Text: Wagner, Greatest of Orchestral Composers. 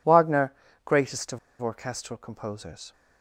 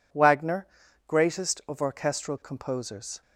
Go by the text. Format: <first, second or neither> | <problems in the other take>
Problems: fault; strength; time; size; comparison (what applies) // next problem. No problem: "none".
second | pauses between "of" and "Orchestral"; slight; at 1.3 s; 0.22 s long